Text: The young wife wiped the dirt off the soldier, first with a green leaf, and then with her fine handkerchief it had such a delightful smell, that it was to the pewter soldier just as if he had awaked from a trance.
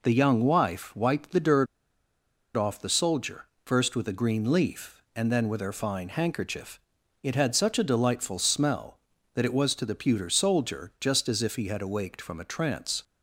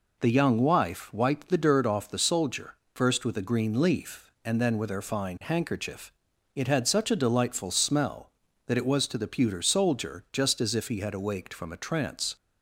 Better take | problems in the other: second | pauses between "dirt" and "off"; noticeable; at 1.6 s; 0.88 s long // pauses between "handkerchief" and "it"; at 6.7 s; 0.44 s long; also in the second

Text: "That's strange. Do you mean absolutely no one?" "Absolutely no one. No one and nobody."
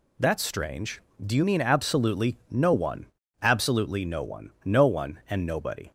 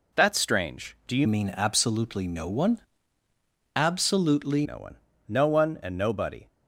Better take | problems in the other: first | changes voice from "mean" to "Absolutely"; from 1.2 to 4.6 s; 3.4 s long

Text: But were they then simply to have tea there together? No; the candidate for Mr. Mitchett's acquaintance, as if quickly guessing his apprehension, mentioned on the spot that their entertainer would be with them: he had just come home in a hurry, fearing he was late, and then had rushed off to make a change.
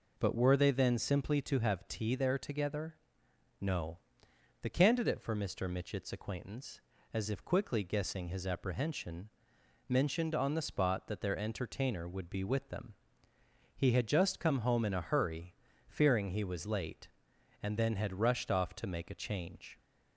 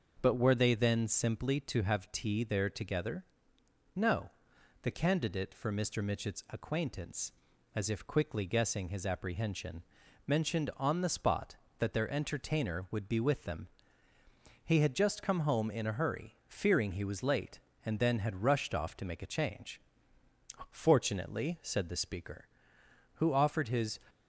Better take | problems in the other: first | goes on to say "Fortunately said the speaker who offered his"; strong; from 20.7 s on; 3.2 s long

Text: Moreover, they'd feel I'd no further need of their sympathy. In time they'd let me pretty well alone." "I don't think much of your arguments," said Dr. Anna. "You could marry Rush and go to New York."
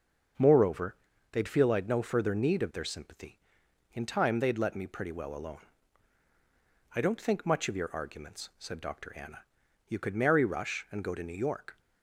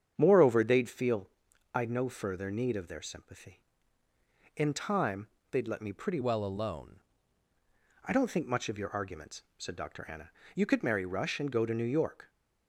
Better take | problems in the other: first | starts louder than the rest; strong; until 1.1 s; 8 dB; also in the first // pauses between "feel" and "I'd"; noticeable; at 1.2 s; 0.46 s long // pauses between "time" and "they'd"; slight; at 5.2 s; 0.22 s long // changes voice from "well" to "alone"; from 6.2 to 6.9 s; 0.7 s long

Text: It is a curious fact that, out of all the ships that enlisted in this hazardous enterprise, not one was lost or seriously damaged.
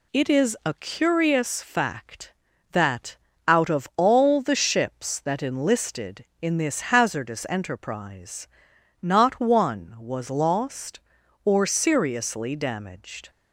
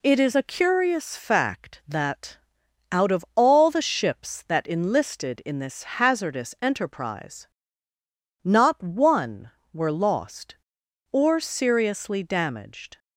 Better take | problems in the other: first | pauses between "this" and "hazardous"; slight; at 5.8 s; 0.16 s long // says "were" for "was"; at 9.7 s

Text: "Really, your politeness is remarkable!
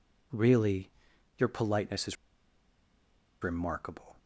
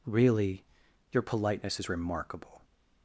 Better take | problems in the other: second | pauses between "is" and "remarkable"; strong; at 2.1 s; 1.2 s long

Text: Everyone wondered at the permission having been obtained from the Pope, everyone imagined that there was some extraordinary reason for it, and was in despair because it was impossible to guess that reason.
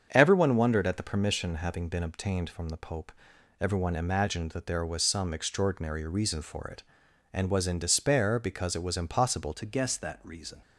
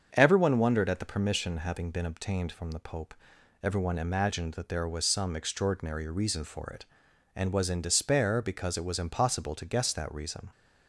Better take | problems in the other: second | starts louder than the rest; strong; until 1.1 s; 7.5 dB; strong in the second // changes voice at "to"; from 9.5 s on; 1.1 s long

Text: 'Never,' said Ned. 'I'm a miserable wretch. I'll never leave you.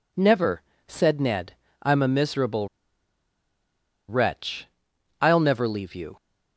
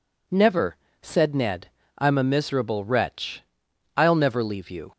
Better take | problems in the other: second | pauses between "miserable" and "wretch"; strong; at 2.6 s; 1.4 s long

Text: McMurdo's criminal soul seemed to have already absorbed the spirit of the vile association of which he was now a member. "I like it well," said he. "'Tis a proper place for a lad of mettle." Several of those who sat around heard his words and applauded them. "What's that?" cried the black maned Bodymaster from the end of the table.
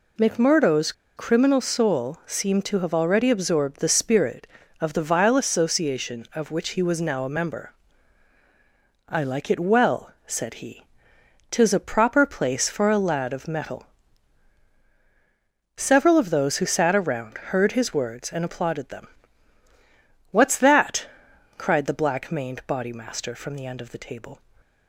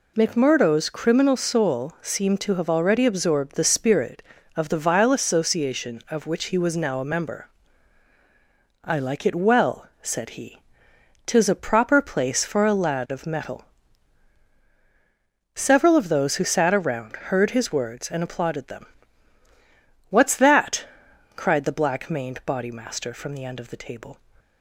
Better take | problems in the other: second | pauses between "McMurdo's" and "criminal"; slight; at 0.9 s; 0.24 s long

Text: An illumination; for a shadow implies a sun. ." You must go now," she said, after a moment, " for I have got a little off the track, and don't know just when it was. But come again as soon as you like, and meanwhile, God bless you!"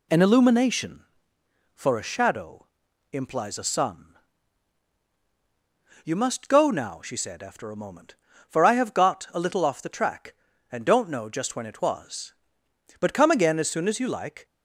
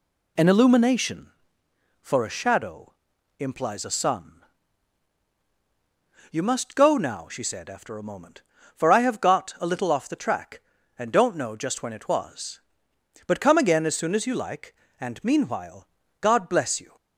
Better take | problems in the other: second | pauses between "shadow" and "implies"; noticeable; at 2.6 s; 0.46 s long; noticeable in the second // stops before "and meanwhile God bless you"; at 14.4 s

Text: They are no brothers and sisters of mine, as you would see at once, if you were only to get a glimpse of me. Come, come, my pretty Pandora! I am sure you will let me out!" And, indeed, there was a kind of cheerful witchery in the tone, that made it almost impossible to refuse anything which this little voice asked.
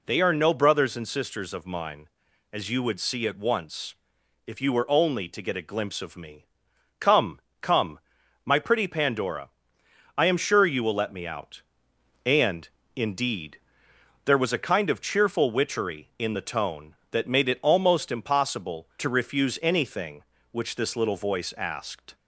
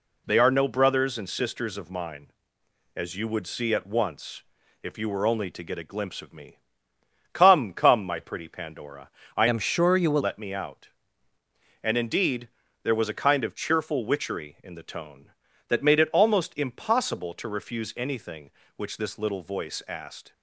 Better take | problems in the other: first | changes voice from "am" to "will"; from 9.4 to 10.2 s; 0.8 s long

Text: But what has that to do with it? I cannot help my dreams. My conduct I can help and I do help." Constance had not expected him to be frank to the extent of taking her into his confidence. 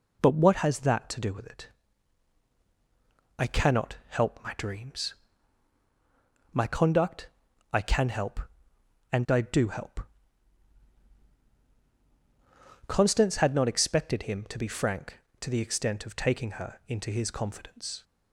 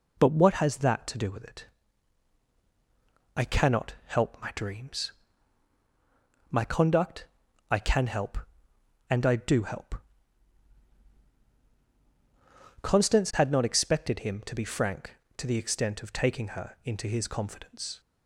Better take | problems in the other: neither | pauses between "conduct" and "I"; the same in both

